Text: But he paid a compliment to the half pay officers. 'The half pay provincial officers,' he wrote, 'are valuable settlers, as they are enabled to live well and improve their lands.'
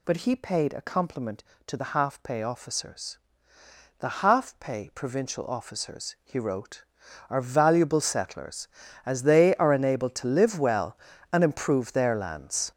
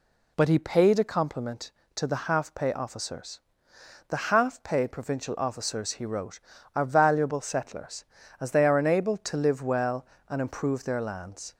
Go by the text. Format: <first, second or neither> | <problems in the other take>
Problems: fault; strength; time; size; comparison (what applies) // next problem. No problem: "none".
second | gets louder; strong; throughout; 8.5 dB